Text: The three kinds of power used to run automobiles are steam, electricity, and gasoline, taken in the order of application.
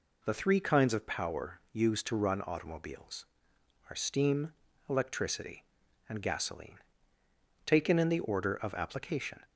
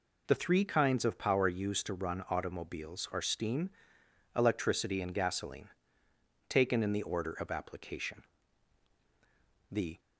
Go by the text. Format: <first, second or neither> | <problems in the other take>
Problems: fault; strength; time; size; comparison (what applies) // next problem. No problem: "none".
first | goes on to say "The"; slight; from 9.6 s on; 0.30 s long